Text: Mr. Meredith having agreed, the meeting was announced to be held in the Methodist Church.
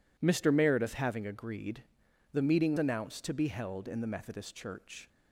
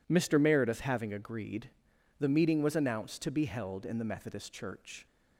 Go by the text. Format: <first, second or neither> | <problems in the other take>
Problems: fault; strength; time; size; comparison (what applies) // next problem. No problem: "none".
second | skips "was"; at 2.7 s